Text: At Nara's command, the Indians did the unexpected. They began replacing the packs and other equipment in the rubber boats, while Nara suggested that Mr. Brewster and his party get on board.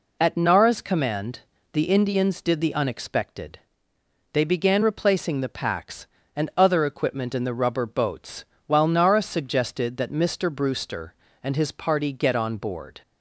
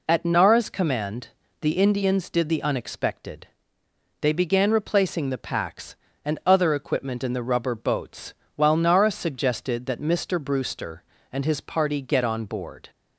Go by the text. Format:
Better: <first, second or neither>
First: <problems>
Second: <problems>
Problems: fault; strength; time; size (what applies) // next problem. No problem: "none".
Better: neither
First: none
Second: none